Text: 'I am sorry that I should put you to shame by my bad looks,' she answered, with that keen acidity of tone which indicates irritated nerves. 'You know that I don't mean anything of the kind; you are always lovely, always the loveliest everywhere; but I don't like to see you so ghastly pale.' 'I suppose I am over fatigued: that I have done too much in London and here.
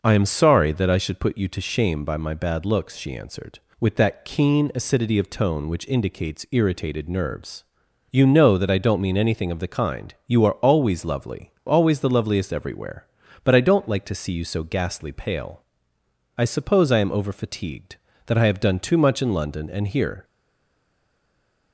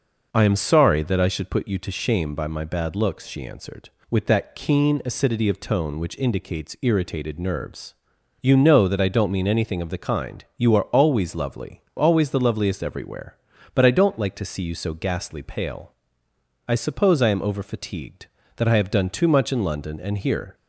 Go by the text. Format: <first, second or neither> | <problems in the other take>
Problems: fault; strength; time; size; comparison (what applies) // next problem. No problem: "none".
second | stays silent after the last word; noticeable; from 20.2 s on; 1.5 s long